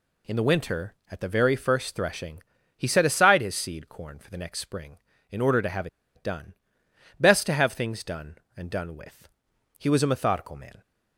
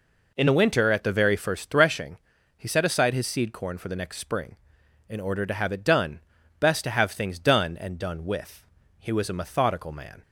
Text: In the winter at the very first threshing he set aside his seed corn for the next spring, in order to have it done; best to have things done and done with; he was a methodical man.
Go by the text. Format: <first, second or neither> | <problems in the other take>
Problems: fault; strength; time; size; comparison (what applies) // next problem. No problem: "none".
second | pauses between "threshing" and "he"; slight; at 2.4 s; 0.36 s long; also in the second // pauses between "have" and "it"; slight; at 5.8 s; 0.28 s long